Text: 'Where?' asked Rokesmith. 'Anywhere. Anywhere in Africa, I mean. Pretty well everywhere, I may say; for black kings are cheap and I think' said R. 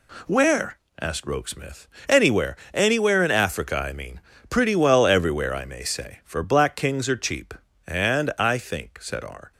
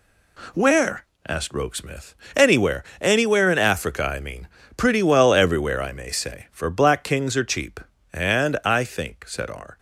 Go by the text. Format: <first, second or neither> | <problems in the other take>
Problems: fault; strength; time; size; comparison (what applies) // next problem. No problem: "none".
neither | none